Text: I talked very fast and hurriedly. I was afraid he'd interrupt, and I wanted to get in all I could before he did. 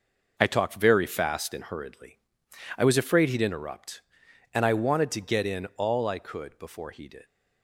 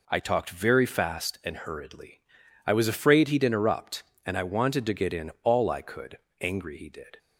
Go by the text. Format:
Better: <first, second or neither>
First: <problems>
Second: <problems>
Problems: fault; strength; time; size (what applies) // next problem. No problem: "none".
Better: first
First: none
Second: says "angry" for "before"; at 6.4 s